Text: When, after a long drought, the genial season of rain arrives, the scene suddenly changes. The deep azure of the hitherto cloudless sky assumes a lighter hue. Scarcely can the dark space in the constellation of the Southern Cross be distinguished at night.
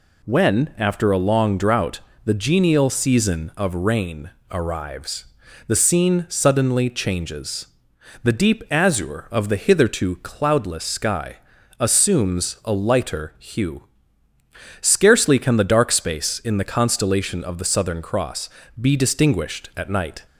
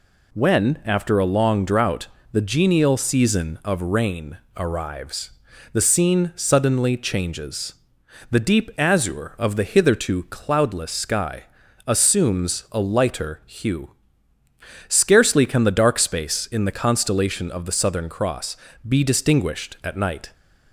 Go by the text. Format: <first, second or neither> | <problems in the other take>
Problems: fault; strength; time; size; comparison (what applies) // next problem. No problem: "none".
neither | pauses between "rain" and "arrives"; slight; the same in both // pauses between "sky" and "assumes"; the same in both // pauses between "Cross" and "be"; slight; the same in both